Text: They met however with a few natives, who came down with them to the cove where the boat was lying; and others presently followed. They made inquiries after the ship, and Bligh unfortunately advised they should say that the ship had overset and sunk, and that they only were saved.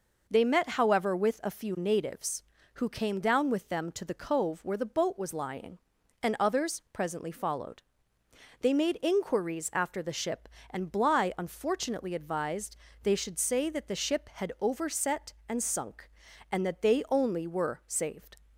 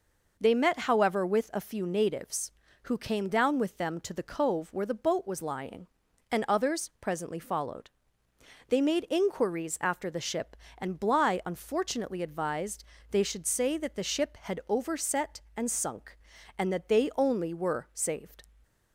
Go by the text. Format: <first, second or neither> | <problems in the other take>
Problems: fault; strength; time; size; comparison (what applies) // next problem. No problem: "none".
neither | pauses between "advised" and "they"; slight; the same in both